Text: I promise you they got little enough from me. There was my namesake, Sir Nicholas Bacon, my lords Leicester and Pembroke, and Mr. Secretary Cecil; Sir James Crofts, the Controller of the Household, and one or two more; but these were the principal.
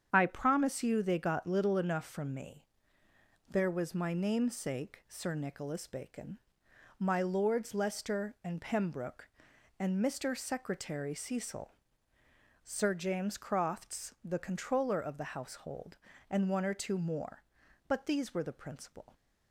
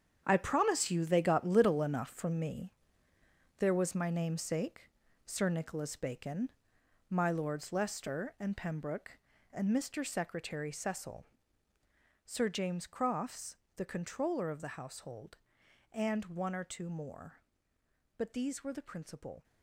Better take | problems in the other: first | gets quieter; strong; throughout; 12 dB // starts louder than the rest; strong; until 1.2 s; 8 dB; strong in the first

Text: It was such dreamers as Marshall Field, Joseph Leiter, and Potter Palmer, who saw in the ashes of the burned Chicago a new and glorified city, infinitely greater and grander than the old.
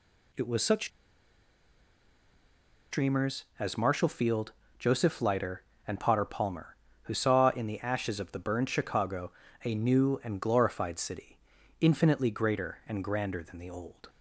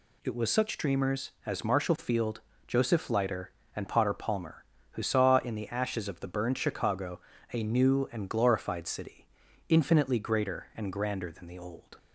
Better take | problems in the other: second | pauses between "such" and "dreamers"; strong; at 0.8 s; 2.0 s long // pauses between "Chicago" and "a"; slight; at 9.3 s; 0.32 s long; slight in the second

